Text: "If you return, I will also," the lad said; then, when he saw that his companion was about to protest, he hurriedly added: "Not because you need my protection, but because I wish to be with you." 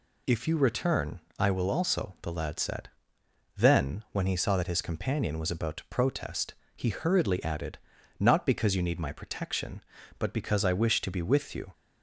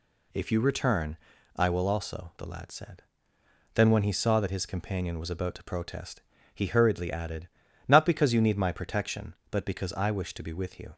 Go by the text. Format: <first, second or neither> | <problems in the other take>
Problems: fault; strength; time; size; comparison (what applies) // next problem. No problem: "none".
neither | none